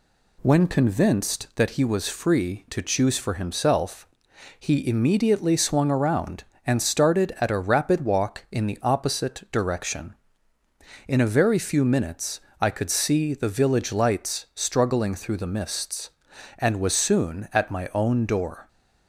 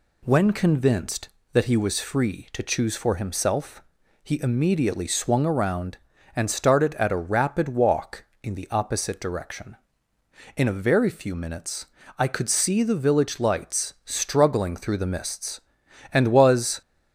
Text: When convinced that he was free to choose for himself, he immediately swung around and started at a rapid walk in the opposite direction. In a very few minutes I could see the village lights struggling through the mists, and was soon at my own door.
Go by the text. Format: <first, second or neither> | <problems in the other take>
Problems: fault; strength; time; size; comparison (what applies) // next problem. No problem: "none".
first | pauses between "minutes" and "I"; slight; at 11.8 s; 0.30 s long; slight in the first // stops before "soon at my own door"; at 16.8 s